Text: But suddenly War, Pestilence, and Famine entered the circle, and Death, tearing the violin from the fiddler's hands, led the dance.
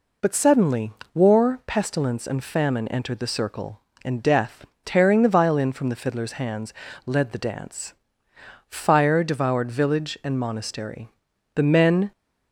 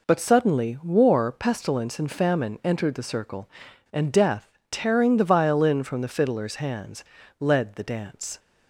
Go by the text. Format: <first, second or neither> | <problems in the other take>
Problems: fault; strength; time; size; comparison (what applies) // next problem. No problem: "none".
second | pauses between "suddenly" and "War"; slight; at 0.9 s; 0.22 s long // goes on to say "Fire devoured village and monastery The men"; strong; from 8.6 s on; 3.4 s long